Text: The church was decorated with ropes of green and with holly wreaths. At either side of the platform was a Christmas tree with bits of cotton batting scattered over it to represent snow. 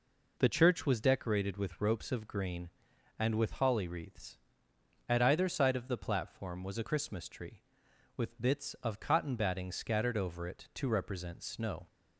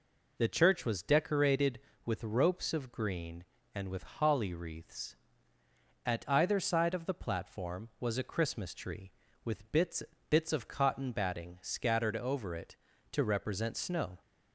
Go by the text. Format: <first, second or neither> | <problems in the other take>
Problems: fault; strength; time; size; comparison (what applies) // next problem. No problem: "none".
first | says "bits" twice; at 10.2 s